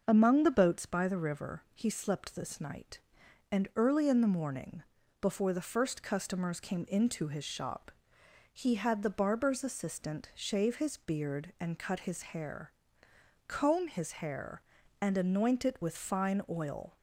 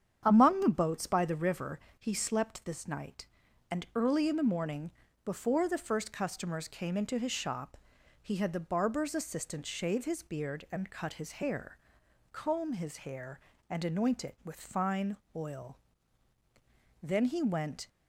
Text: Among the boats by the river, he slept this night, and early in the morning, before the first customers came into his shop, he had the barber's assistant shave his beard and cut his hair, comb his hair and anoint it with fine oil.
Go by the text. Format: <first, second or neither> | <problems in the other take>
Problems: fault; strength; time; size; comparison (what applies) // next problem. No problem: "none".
first | starts louder than the rest; strong; until 1.2 s; 8.5 dB; noticeable in the first // pauses between "fine" and "oil"; slight; at 15.1 s; 0.16 s long // goes on to say "Then he went"; noticeable; from 17.0 s on; 0.86 s long